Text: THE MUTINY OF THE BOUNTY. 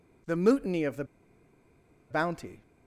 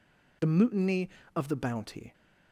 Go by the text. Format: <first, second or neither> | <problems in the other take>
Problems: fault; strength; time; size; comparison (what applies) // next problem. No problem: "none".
second | pauses between "THE" and "BOUNTY"; at 1.0 s; 1.0 s long